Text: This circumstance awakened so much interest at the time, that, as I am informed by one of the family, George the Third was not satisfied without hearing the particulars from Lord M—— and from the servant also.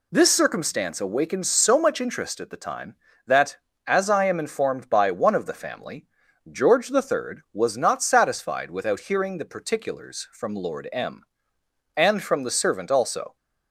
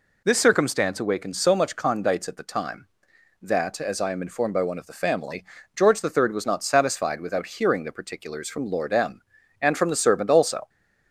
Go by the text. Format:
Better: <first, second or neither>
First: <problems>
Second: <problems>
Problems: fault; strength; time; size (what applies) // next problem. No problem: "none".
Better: first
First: none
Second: says "condites" for "interest"; at 1.7 s